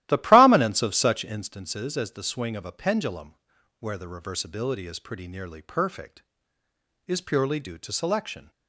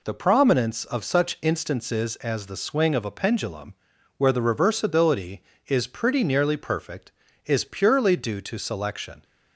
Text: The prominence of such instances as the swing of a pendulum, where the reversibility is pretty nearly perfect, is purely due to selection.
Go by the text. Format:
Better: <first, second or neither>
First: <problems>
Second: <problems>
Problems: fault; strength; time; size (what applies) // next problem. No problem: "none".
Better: second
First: starts louder than the rest; strong; until 1.5 s; 14.5 dB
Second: none